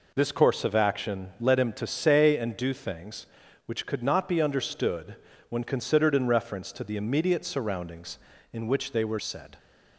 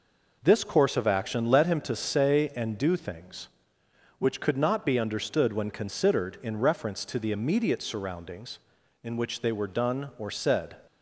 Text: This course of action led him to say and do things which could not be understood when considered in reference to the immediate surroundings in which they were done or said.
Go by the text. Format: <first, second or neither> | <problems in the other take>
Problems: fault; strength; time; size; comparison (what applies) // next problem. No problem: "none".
second | pauses between "understood" and "when"; slight; at 5.1 s; 0.34 s long // skips "done or"; at 9.1 s